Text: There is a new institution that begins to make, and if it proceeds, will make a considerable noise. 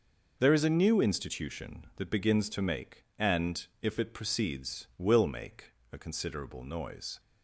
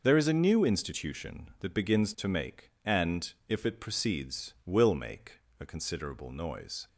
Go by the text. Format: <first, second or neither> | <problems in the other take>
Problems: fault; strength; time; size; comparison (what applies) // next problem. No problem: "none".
neither | pauses between "and" and "if"; slight; the same in both // pauses between "make" and "a"; slight; the same in both